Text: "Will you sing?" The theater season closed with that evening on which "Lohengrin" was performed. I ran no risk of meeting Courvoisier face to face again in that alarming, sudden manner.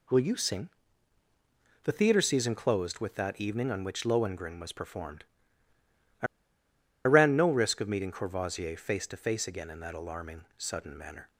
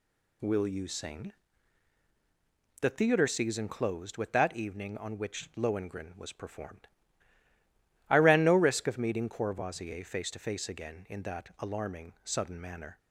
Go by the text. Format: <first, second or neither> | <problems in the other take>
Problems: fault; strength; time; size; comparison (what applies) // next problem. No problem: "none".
second | pauses between "I" and "ran"; noticeable; at 6.2 s; 0.79 s long